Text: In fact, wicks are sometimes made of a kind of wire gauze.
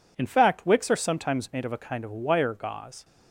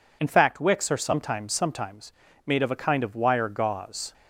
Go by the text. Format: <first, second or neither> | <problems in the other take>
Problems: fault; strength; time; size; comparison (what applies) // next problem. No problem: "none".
first | says "sometimes" twice; at 1.5 s